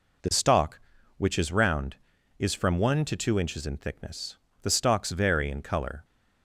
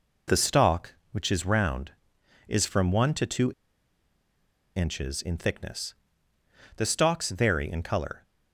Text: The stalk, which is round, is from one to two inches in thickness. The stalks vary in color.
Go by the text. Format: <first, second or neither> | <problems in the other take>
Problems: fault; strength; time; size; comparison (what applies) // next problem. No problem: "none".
first | pauses between "two" and "inches"; strong; at 3.5 s; 1.2 s long